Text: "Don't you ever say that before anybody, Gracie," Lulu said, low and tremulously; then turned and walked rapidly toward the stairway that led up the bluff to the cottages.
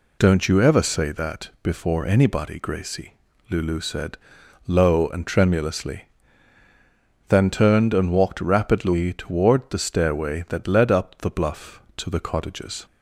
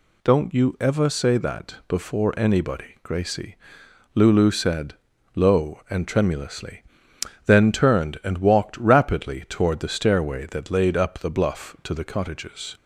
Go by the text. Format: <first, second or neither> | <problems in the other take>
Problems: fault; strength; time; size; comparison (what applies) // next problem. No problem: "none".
first | says "laid" for "led"; at 10.7 s